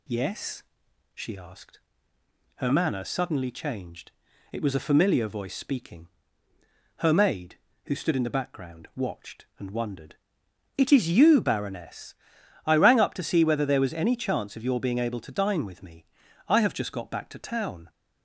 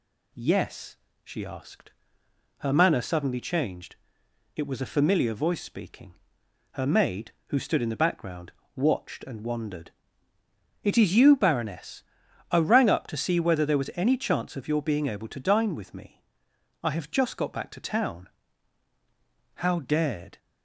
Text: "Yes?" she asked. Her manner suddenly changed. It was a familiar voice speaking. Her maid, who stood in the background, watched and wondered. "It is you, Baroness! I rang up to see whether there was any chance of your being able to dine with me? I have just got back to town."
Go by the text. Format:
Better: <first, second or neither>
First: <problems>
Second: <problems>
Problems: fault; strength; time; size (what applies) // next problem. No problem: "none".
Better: first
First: none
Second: goes on to say "How dared"; noticeable; from 19.5 s on; 0.84 s long